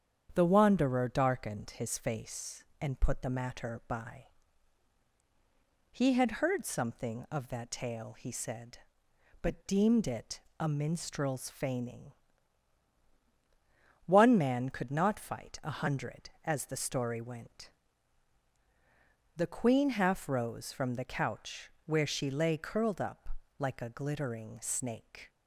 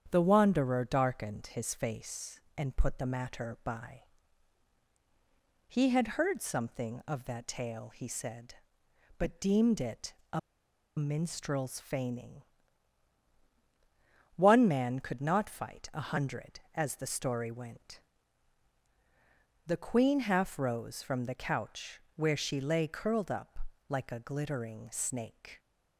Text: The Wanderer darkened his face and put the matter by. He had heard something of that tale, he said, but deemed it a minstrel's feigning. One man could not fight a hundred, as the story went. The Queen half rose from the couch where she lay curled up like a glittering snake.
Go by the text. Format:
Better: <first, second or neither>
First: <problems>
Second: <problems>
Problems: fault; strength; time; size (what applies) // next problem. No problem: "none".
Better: first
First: starts louder than the rest; strong; until 1.3 s; 8.5 dB // pauses between "it" and "a"; slight; at 10.3 s; 0.18 s long // pauses between "couch" and "where"; slight; at 21.6 s; 0.16 s long // pauses between "up" and "like"; slight; at 23.2 s; 0.30 s long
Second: starts louder than the rest; strong; until 1.1 s; 8.5 dB // pauses between "it" and "a"; slight; at 10.1 s; 0.18 s long // pauses between "a" and "minstrel's"; noticeable; at 10.3 s; 0.57 s long // pauses between "couch" and "where"; slight; at 21.9 s; 0.16 s long // pauses between "up" and "like"; slight; at 23.5 s; 0.30 s long